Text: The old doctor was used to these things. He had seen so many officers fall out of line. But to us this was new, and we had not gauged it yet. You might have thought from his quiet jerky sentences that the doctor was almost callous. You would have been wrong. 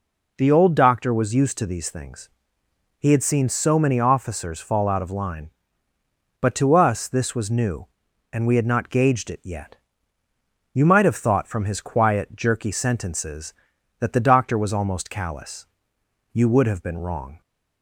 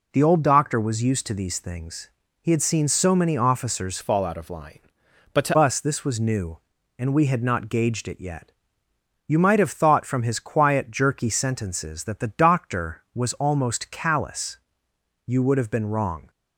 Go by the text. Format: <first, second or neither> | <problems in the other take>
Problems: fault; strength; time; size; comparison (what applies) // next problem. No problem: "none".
first | changes voice from "fall" to "to"; from 4.0 to 5.5 s; 1.5 s long